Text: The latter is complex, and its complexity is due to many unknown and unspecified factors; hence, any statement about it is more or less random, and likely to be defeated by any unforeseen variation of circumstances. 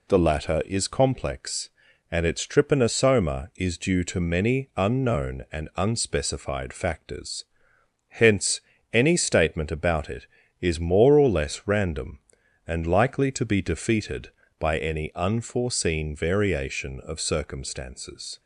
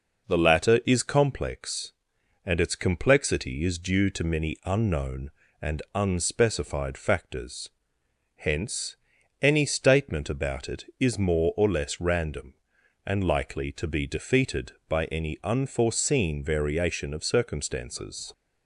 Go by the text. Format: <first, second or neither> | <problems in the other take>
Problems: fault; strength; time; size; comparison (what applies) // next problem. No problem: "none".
second | says "trypanosoma" for "complexity"; at 2.4 s